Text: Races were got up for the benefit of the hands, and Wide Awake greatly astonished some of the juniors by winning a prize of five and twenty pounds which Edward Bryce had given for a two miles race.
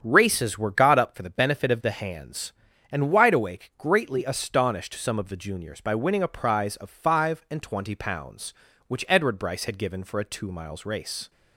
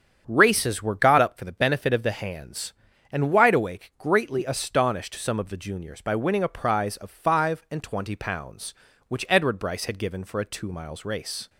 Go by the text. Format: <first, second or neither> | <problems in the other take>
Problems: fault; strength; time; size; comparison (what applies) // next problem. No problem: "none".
neither | starts louder than the rest; strong; the same in both